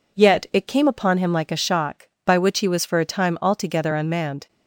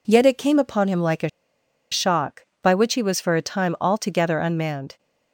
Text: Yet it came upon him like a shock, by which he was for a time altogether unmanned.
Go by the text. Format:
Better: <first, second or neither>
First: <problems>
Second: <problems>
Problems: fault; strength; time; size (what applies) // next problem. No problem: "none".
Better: first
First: none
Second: pauses between "a" and "shock"; noticeable; at 1.2 s; 0.63 s long